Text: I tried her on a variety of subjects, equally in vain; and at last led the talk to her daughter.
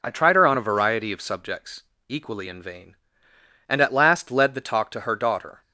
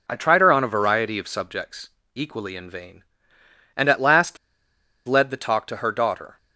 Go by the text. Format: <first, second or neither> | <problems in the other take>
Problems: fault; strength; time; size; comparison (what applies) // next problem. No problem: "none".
first | pauses between "last" and "led"; noticeable; at 4.3 s; 0.69 s long